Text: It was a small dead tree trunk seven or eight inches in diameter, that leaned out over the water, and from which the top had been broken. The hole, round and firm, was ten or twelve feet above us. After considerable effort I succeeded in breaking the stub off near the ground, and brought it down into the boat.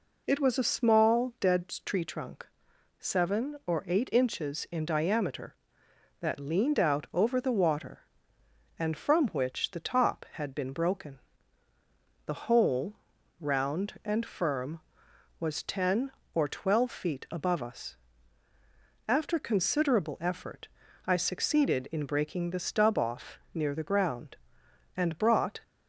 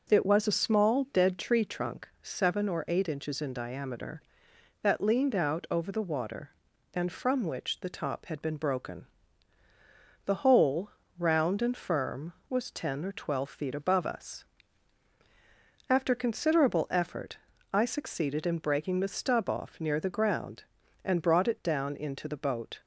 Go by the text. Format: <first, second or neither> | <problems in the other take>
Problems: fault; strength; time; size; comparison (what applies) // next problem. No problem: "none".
second | pauses between "trunk" and "seven"; noticeable; at 2.4 s; 0.52 s long // pauses between "effort" and "I"; slight; at 20.6 s; 0.36 s long; slight in the second // stops before "it down into the boat"; at 25.6 s